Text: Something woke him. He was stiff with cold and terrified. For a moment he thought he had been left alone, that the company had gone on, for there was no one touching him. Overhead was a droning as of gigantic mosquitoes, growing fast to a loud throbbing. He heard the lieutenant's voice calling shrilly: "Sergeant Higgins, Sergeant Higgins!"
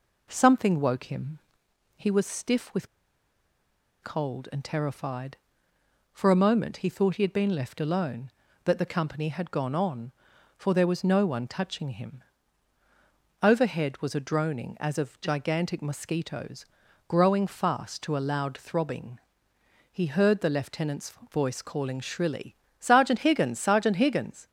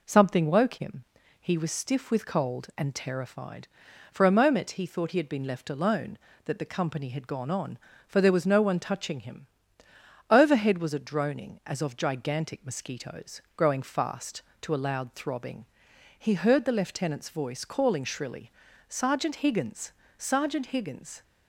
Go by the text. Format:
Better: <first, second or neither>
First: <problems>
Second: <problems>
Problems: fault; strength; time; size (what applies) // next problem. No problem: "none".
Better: second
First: pauses between "with" and "cold"; at 2.8 s; 1.1 s long // pauses between "lieutenant's" and "voice"; slight; at 21.1 s; 0.18 s long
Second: none